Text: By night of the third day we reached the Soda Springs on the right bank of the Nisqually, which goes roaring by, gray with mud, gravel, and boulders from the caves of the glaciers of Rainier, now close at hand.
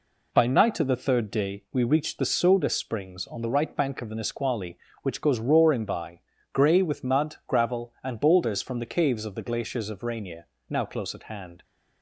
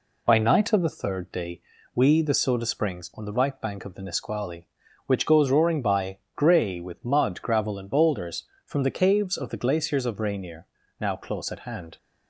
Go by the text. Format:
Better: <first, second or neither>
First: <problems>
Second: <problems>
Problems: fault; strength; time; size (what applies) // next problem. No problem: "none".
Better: first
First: none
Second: pauses between "day" and "we"; slight; at 1.6 s; 0.34 s long // skips "reached"; at 2.2 s